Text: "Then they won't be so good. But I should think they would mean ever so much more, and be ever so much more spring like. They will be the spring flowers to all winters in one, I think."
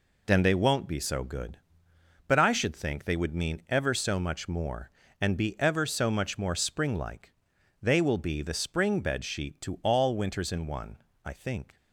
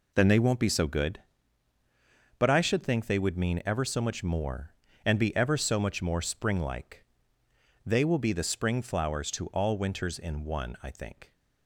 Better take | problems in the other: second | says "bedsheet" for "flowers"; at 9.0 s

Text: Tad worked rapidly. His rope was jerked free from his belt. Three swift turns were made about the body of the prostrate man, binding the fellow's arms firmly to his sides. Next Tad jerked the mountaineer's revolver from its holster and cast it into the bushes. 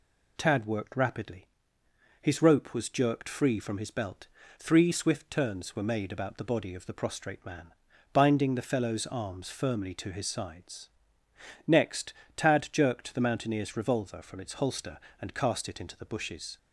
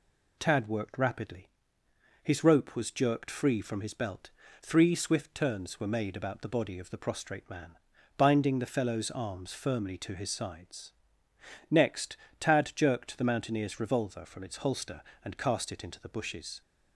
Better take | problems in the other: neither | pauses between "Next" and "Tad"; slight; the same in both

